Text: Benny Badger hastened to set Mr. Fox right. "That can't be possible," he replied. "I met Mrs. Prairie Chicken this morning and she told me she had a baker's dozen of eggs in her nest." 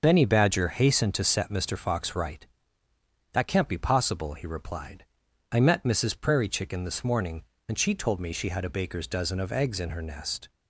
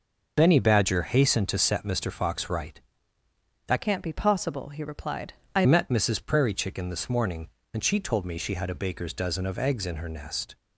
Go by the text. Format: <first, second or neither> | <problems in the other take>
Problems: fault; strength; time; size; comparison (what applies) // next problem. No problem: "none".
first | changes voice from "can't" to "I"; from 3.8 to 5.6 s; 1.8 s long